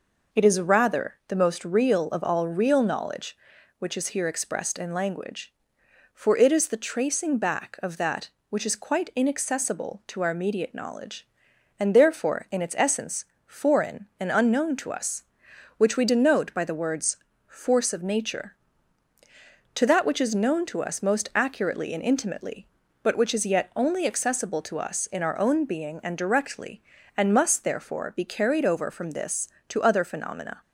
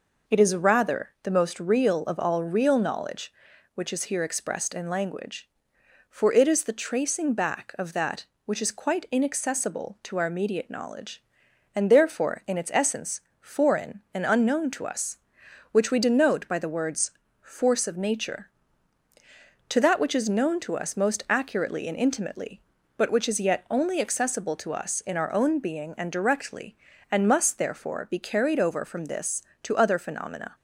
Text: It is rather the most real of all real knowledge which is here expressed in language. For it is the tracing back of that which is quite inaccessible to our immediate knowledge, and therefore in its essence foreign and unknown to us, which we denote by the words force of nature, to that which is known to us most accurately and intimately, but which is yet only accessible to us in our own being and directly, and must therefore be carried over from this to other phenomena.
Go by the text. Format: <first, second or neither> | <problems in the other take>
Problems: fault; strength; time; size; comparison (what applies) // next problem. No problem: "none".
neither | pauses between "essence" and "foreign"; slight; the same in both // pauses between "words" and "force"; slight; the same in both